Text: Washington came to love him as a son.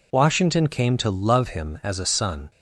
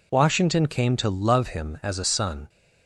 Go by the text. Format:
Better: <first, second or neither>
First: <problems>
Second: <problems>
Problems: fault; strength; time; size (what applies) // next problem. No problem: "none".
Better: neither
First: none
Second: none